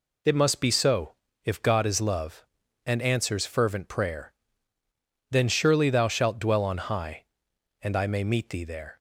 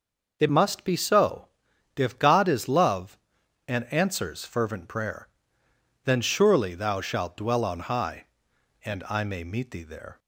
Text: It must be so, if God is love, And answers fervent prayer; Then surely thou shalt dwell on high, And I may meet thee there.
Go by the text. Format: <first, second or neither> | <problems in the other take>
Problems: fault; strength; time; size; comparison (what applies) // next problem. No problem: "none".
first | changes voice at "must"; from 0.4 s on; 9.7 s long